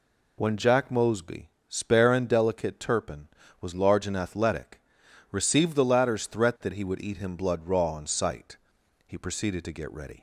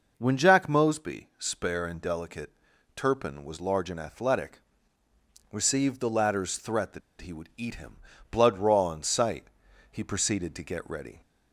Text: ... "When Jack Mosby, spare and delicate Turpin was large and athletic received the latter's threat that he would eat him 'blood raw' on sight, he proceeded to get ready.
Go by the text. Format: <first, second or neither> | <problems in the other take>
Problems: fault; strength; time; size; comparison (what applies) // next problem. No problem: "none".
first | pauses between "delicate" and "Turpin"; at 2.5 s; 0.42 s long // pauses between "athletic" and "received"; noticeable; at 4.6 s; 0.90 s long; noticeable in the first // pauses between "that" and "he"; slight; at 7.0 s; 0.20 s long // pauses between "him" and "blood"; slight; at 7.9 s; 0.34 s long